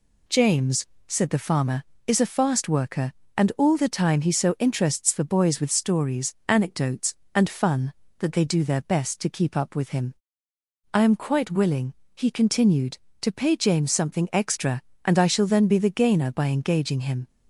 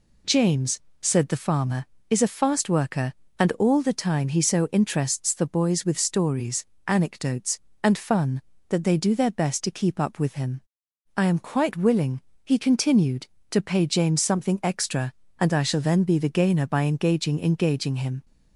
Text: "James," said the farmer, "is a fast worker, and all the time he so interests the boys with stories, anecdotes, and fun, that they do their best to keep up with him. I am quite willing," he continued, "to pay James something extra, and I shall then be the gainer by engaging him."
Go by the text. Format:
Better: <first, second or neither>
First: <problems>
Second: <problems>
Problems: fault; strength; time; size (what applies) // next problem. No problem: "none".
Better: first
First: none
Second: says "engaging" twice; at 17.4 s